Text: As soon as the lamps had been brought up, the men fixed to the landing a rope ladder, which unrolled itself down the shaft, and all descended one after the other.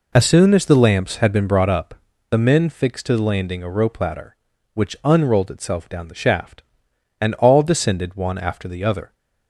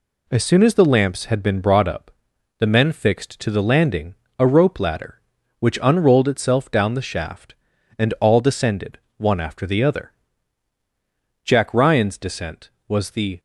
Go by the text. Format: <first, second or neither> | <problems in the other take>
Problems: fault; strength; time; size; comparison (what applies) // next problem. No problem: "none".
first | pauses between "landing" and "a"; slight; at 4.1 s; 0.24 s long // pauses between "descended" and "one"; slight; at 8.9 s; 0.20 s long // goes on to say "Jack Ryan's descent was the"; strong; from 11.4 s on; 1.9 s long